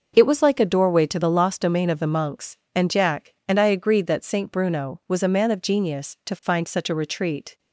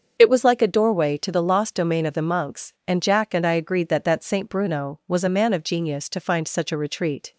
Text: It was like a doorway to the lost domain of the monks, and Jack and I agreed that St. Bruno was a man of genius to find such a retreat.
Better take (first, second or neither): first